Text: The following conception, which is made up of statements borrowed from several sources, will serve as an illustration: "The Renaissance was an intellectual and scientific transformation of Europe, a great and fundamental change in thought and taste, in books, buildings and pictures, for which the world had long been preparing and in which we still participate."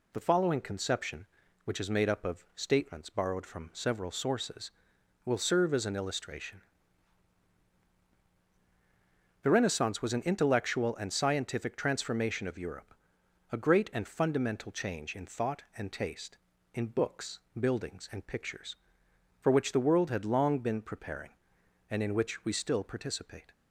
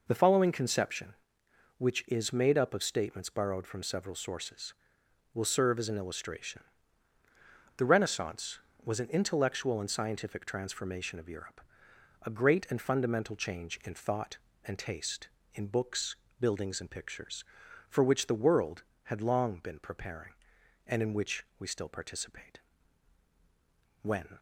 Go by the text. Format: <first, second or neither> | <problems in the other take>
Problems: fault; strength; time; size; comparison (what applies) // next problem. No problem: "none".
first | goes on to say "When"; slight; from 24.0 s on; 0.36 s long